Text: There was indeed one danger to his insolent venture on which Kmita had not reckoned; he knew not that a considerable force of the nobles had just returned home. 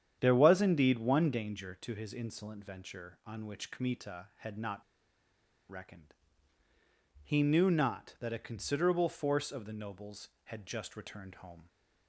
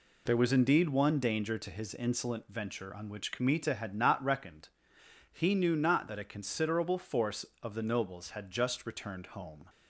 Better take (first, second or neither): second